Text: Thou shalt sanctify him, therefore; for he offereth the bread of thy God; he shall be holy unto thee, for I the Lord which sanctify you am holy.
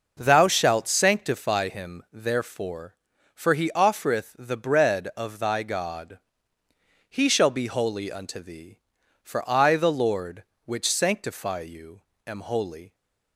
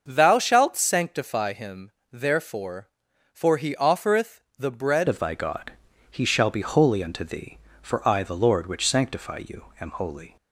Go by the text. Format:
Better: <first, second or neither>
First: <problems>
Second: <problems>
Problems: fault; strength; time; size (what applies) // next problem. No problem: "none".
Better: first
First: pauses between "you" and "am"; slight; at 12.0 s; 0.26 s long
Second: starts louder than the rest; until 1.0 s; 6.5 dB // pauses between "offereth" and "the"; slight; at 4.3 s; 0.18 s long // changes voice at "of"; from 5.0 s on; 5.3 s long // pauses between "you" and "am"; slight; at 9.6 s; 0.16 s long